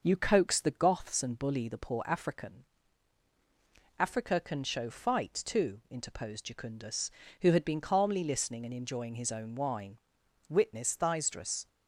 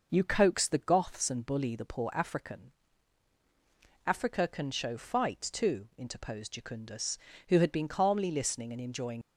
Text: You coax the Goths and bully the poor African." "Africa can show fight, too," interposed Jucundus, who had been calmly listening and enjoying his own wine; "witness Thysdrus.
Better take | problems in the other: first | stops before "his own wine witness Thysdrus"; at 9.2 s

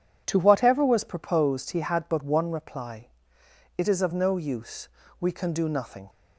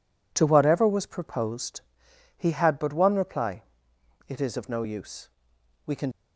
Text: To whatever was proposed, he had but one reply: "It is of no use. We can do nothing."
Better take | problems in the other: first | stops before "do nothing"; at 6.1 s

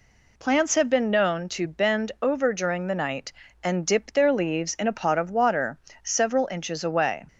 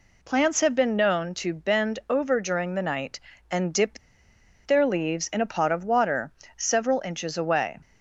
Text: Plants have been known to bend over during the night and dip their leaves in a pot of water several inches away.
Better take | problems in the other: first | pauses between "dip" and "their"; noticeable; at 3.9 s; 0.67 s long // pauses between "water" and "several"; slight; at 6.3 s; 0.26 s long; slight in the first

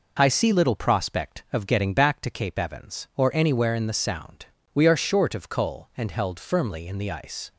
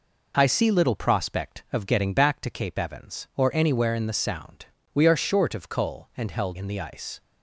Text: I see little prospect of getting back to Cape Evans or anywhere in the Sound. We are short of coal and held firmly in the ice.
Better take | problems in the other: first | skips "firmly"; at 6.5 s

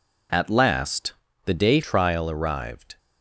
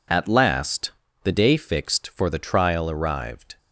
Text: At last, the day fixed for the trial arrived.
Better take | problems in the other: second | skips "fixed for the"; at 1.8 s

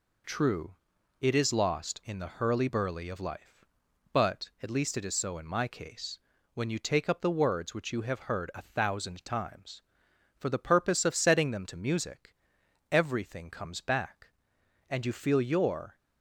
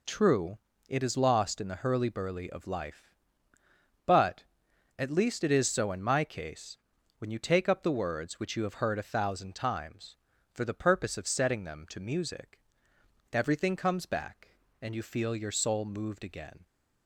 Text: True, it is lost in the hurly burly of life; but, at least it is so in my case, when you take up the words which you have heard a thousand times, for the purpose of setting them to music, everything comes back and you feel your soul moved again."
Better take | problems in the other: second | stops before "soul moved again"; at 15.9 s

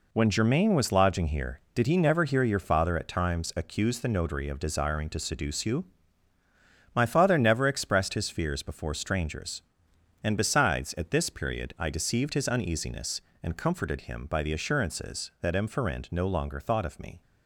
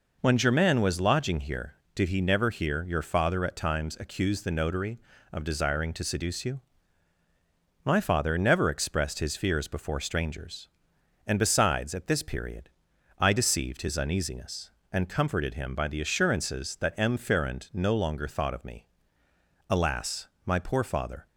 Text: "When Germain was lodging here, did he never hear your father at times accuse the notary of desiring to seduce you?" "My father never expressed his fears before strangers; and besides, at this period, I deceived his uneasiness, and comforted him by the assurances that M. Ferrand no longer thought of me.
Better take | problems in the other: first | goes on to say "Alas my poor father"; from 19.6 s on; 1.5 s long

